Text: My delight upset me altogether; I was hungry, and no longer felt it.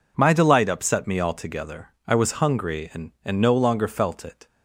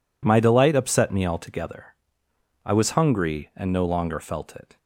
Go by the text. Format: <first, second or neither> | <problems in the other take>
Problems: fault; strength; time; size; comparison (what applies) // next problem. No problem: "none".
second | says "and" twice; at 3.2 s